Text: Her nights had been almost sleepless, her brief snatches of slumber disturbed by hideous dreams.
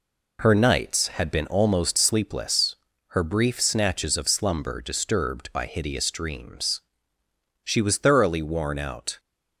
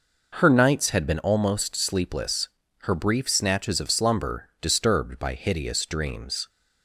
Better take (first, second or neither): second